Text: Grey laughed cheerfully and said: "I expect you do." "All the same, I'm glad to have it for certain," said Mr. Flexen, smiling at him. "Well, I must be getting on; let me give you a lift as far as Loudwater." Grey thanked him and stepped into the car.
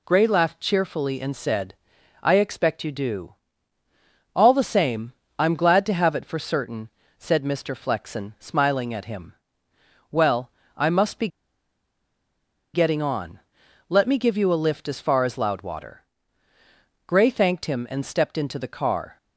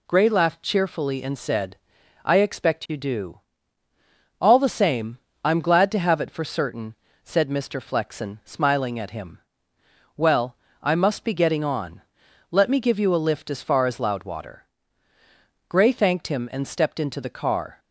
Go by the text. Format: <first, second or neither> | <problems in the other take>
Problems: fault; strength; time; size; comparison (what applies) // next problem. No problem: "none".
second | pauses between "be" and "getting"; strong; at 11.2 s; 1.4 s long